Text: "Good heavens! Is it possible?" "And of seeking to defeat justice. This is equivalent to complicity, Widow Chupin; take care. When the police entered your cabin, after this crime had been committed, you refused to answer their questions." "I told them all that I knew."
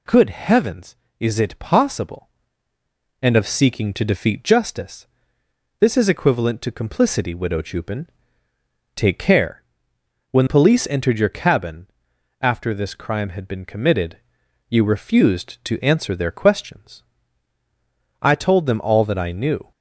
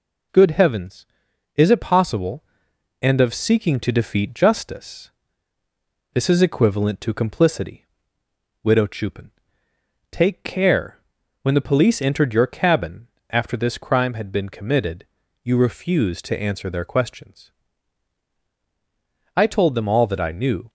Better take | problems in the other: second | skips "the"; at 10.4 s

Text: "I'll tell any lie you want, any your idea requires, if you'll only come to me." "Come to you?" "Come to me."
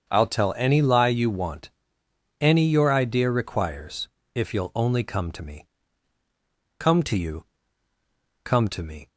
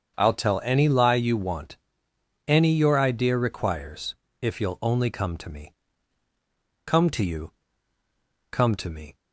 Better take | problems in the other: neither | starts louder than the rest; the same in both

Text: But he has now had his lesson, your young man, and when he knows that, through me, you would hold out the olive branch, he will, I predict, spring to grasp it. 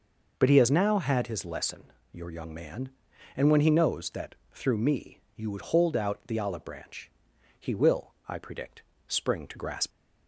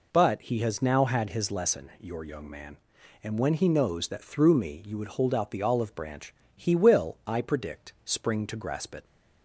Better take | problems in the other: second | stops before "it"; at 9.9 s

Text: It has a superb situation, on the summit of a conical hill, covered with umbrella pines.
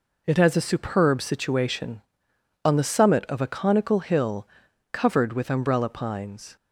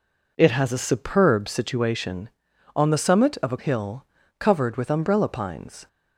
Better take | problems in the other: first | skips "conical"; at 3.5 s

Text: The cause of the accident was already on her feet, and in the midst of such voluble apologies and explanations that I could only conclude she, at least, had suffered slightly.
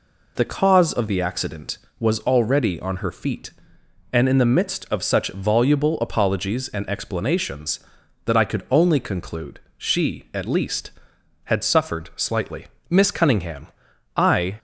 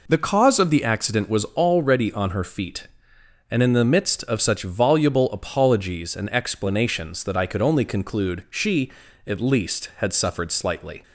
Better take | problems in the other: second | pauses between "conclude" and "she"; slight; at 9.6 s; 0.18 s long // goes on to say "Miss Cunningham I"; strong; from 12.9 s on; 1.6 s long

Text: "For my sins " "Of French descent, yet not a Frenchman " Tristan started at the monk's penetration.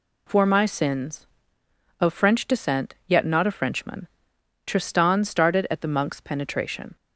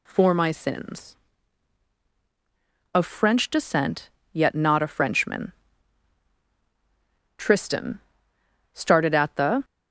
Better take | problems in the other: first | pauses between "Tristan" and "started"; noticeable; at 7.9 s; 0.74 s long // stops before "monk's penetration"; at 9.6 s

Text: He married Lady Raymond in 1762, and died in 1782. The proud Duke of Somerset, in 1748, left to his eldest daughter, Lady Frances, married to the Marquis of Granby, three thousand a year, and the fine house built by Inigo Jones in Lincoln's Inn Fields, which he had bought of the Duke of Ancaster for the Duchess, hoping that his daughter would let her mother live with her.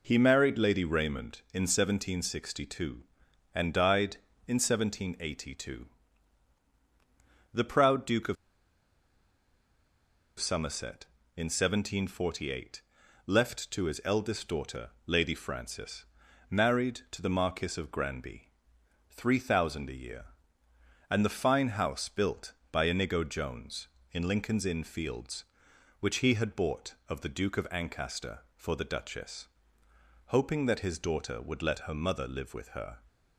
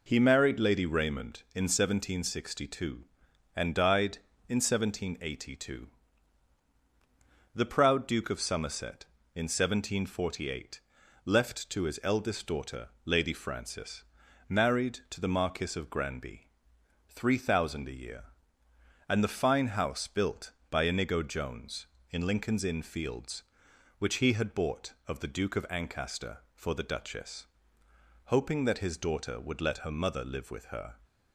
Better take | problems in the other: second | pauses between "of" and "Somerset"; strong; at 8.3 s; 2.0 s long

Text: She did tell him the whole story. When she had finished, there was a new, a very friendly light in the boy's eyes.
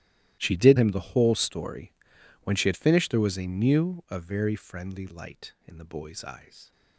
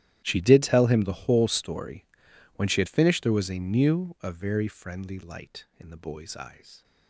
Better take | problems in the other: second | starts louder than the rest; strong; until 1.3 s; 14 dB; strong in the second // skips "tell"; at 0.7 s

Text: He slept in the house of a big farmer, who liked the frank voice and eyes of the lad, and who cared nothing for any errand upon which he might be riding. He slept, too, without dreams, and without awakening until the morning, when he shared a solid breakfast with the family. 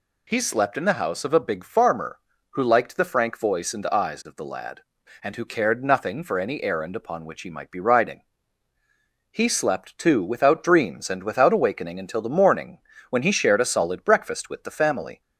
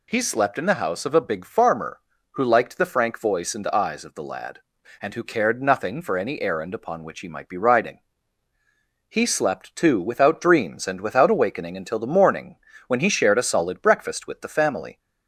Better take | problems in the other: neither | none

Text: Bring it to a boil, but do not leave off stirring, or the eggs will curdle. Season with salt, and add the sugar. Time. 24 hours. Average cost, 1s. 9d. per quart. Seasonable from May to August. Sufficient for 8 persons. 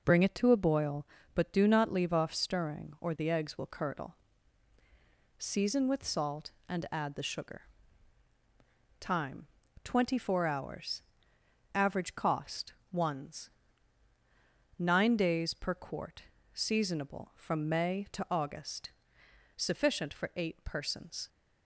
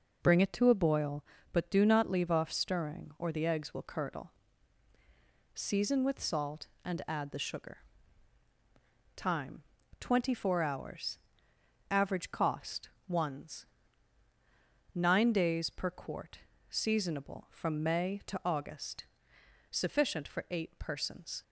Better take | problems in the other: neither | none

